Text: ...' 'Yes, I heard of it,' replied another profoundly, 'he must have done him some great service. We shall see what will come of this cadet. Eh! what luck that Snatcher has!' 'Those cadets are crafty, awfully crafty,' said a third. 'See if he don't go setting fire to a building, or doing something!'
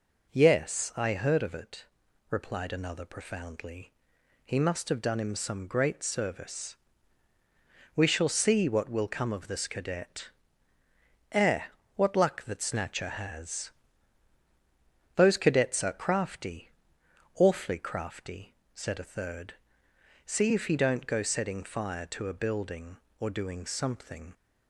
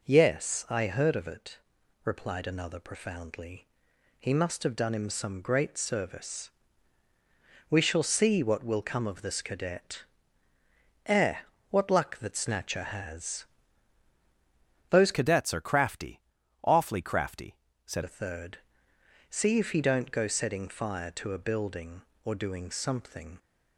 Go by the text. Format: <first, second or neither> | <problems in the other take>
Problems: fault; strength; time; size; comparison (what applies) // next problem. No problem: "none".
first | changes voice from "cadets" to "said"; from 15.1 to 18.0 s; 2.9 s long